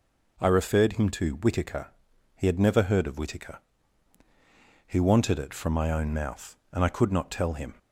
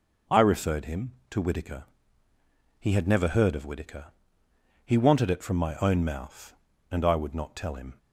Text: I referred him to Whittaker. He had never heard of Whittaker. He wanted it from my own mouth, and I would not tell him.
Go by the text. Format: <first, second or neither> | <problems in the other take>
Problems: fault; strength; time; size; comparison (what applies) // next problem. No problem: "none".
second | says "could" for "would"; at 6.8 s